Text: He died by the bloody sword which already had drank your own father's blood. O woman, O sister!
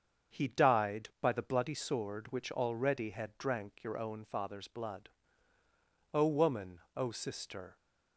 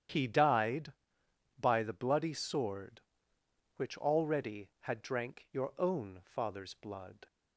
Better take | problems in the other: first | starts louder than the rest; strong; until 1.7 s; 10 dB; also in the first // stops before "O woman O sister"; at 7.2 s

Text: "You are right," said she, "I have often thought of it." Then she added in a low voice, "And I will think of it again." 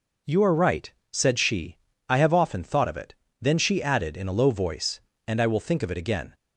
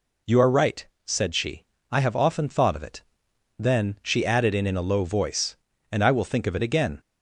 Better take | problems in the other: first | says "in" twice; at 4.6 s

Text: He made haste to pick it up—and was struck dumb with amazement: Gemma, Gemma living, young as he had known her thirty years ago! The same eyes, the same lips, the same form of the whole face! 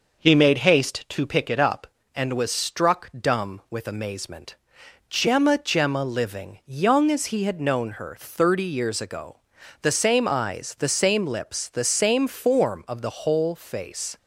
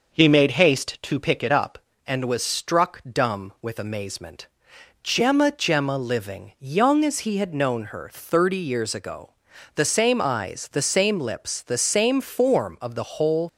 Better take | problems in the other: first | stops before "face"; at 13.4 s

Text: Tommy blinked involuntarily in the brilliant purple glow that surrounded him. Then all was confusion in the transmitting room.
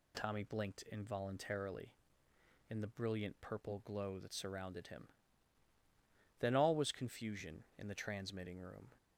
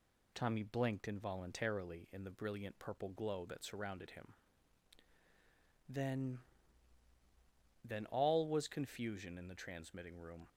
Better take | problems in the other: first | says "Then" twice; at 7.8 s

